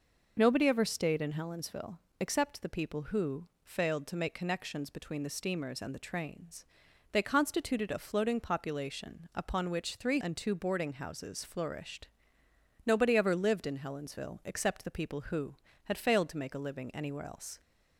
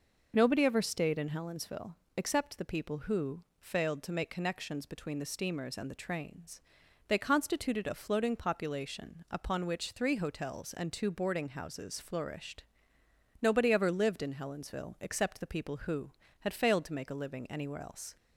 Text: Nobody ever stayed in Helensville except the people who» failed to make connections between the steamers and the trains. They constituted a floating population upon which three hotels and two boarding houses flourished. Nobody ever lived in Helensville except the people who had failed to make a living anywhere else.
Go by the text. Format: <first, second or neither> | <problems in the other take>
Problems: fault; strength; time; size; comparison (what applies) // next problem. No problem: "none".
second | pauses between "Helensville" and "except"; slight; at 1.9 s; 0.22 s long; slight in the second // pauses between "who" and "failed"; slight; at 3.4 s; 0.16 s long; slight in the second // skips "hotels"; at 10.2 s